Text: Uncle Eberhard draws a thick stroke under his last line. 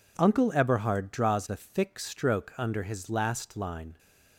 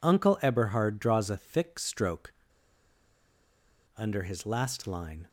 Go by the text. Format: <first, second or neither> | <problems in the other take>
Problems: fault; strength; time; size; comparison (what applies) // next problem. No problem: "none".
first | pauses between "stroke" and "under"; strong; at 2.3 s; 1.6 s long